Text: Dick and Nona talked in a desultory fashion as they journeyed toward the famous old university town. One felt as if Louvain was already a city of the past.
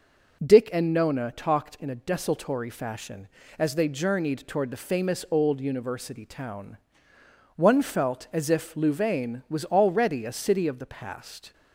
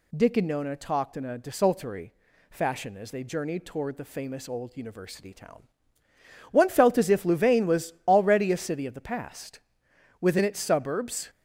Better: first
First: none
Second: pauses between "desultory" and "fashion"; at 2.1 s; 0.38 s long // goes on to say "Within its suburbs"; noticeable; from 10.1 s on; 1.1 s long

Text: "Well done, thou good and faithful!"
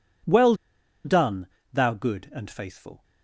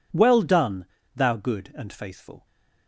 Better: second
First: pauses between "Well" and "done"; noticeable; at 0.5 s; 0.50 s long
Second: none

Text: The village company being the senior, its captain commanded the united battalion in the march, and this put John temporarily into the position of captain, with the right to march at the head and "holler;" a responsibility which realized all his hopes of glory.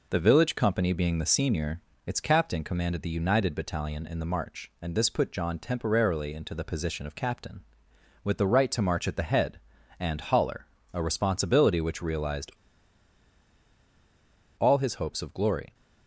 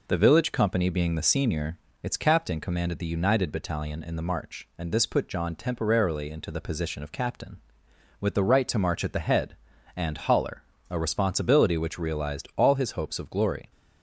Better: second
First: pauses between "realized" and "all"; strong; at 12.5 s; 2.0 s long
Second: none

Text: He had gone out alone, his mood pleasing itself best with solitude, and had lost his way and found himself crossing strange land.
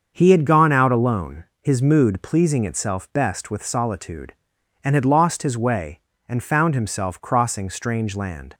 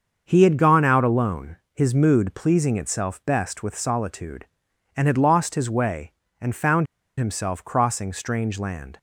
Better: first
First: starts louder than the rest; until 1.1 s; 6.5 dB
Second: starts louder than the rest; until 1.2 s; 6.5 dB // pauses between "found" and "himself"; slight; at 6.8 s; 0.33 s long

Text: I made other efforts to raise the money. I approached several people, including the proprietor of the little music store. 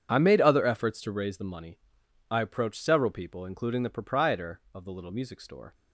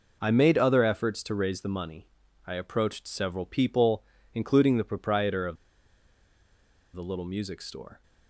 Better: first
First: none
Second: pauses between "of" and "the"; strong; at 5.5 s; 1.3 s long

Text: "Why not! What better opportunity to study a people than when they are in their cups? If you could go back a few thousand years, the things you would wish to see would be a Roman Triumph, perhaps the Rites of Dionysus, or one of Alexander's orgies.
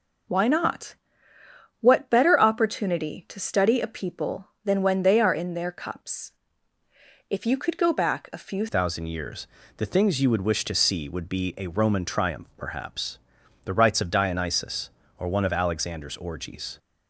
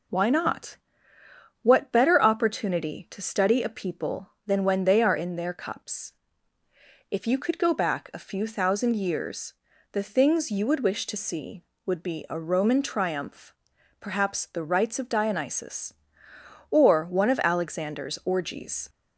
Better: second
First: changes voice at "thousand"; from 8.6 s on; 8.1 s long // pauses between "perhaps" and "the"; noticeable; at 13.1 s; 0.46 s long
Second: none

